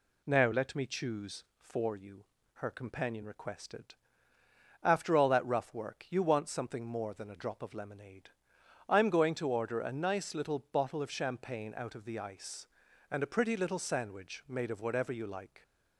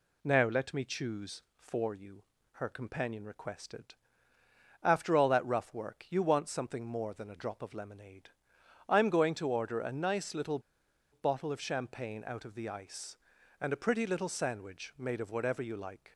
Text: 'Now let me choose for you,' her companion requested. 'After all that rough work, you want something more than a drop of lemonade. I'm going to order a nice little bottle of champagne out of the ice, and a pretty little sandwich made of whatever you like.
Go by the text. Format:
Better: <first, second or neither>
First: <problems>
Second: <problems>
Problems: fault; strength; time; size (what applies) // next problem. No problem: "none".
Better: first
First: none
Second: pauses between "little" and "bottle"; noticeable; at 10.6 s; 0.51 s long